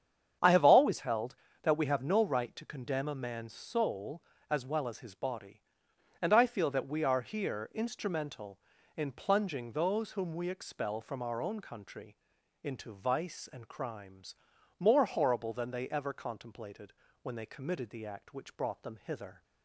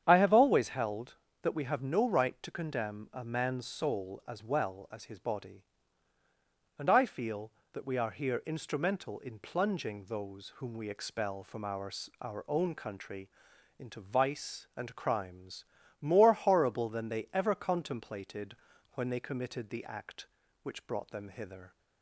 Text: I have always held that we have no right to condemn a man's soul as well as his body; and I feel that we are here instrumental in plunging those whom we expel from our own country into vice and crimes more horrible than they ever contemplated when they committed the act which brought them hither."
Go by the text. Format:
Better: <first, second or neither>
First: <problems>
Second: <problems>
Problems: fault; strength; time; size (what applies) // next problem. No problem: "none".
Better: first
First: starts louder than the rest; strong; until 1.6 s; 8 dB // pauses between "country" and "into"; noticeable; at 12.1 s; 0.48 s long // pauses between "crimes" and "more"; at 14.3 s; 0.42 s long // pauses between "contemplated" and "when"; slight; at 16.9 s; 0.30 s long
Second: starts louder than the rest; strong; until 1.0 s; 9 dB // says "our" twice; at 12.2 s // pauses between "country" and "into"; noticeable; at 13.2 s; 0.50 s long // pauses between "crimes" and "more"; at 15.6 s; 0.38 s long // pauses between "contemplated" and "when"; at 18.5 s; 0.38 s long